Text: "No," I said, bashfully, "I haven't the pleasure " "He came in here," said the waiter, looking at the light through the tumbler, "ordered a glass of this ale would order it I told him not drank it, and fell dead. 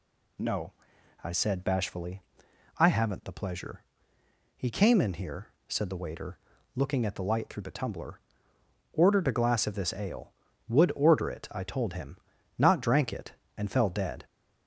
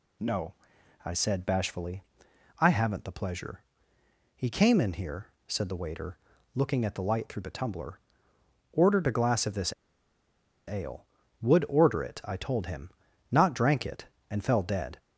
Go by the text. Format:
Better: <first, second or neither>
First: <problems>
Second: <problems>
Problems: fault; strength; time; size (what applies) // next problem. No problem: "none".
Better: first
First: pauses between "him" and "not"; at 12.1 s; 0.40 s long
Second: pauses between "this" and "ale"; noticeable; at 9.7 s; 0.95 s long // pauses between "him" and "not"; at 12.9 s; 0.40 s long